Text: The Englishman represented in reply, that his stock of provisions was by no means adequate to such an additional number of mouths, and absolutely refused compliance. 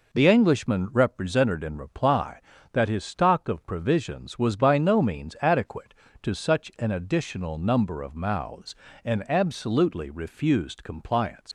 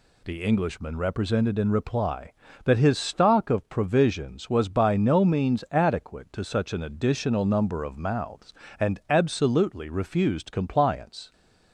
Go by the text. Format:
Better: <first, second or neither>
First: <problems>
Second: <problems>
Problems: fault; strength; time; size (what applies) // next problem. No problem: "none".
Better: second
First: leaves "compliance" unfinished; at 11.4 s; 100 ms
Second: none